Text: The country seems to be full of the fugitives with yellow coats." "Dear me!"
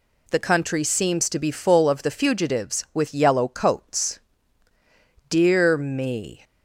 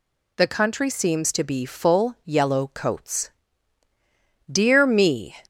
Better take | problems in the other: first | skips "of the fugitives with"; at 2.1 s

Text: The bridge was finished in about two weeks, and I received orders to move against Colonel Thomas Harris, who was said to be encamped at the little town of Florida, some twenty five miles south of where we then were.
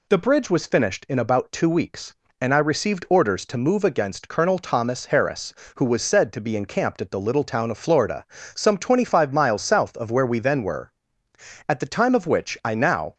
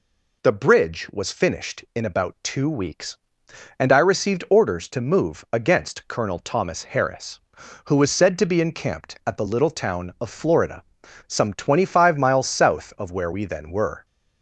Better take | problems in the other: second | goes on to say "At the time of which I now"; from 11.6 s on; 1.4 s long

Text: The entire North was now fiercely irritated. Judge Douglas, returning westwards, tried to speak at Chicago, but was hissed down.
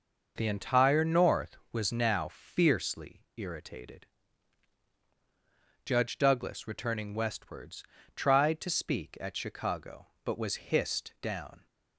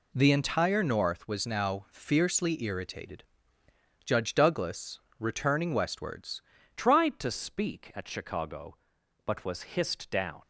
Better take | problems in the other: first | changes voice at "tried"; from 6.7 s on; 3.7 s long

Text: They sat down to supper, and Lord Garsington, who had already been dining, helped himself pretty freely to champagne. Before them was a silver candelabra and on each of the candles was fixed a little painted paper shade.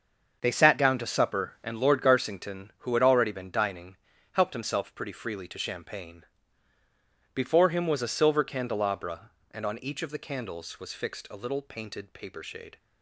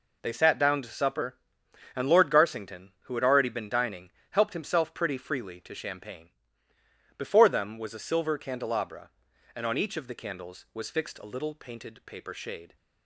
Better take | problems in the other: second | starts louder than the rest; until 1.4 s; 6.5 dB // says "him" for "them"; at 7.6 s

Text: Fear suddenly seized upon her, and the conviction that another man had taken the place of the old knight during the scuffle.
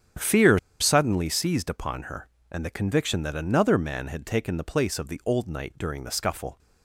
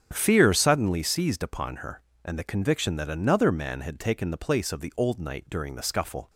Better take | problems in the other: second | starts louder than the rest; strong; until 1.4 s; 8.5 dB; strong in the second // pauses between "Fear" and "suddenly"; slight; at 0.5 s; 0.23 s long

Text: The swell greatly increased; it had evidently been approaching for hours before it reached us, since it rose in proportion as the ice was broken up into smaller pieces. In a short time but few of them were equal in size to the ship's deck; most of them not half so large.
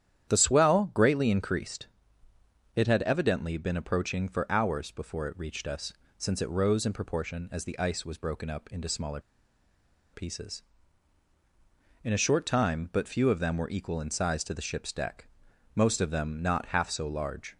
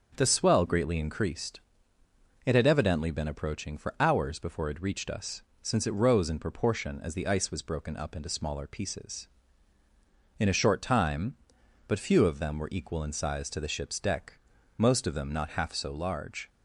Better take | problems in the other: second | starts louder than the rest; strong; until 1.3 s; 10 dB; also in the second // pauses between "smaller" and "pieces"; noticeable; at 9.2 s; 0.91 s long

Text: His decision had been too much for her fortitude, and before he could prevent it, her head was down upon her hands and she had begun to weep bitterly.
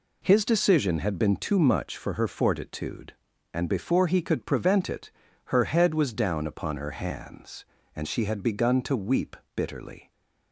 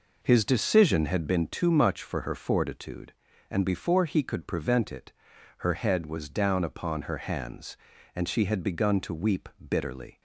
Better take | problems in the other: first | starts louder than the rest; noticeable; until 1.4 s; 5 dB // pauses between "weep" and "bitterly"; slight; at 9.4 s; 0.20 s long; slight in the first

